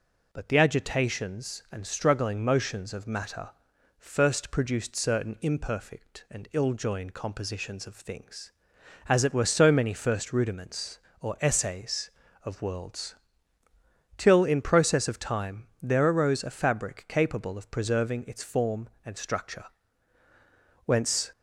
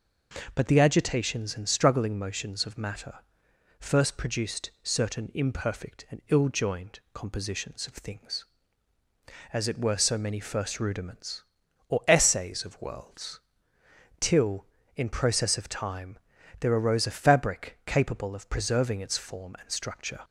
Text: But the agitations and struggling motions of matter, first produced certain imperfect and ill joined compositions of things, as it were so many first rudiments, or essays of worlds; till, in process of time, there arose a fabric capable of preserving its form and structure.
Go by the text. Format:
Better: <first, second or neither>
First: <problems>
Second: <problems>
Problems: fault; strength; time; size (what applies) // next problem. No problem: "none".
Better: second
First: goes on to say "Whence"; slight; from 20.8 s on; 0.46 s long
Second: none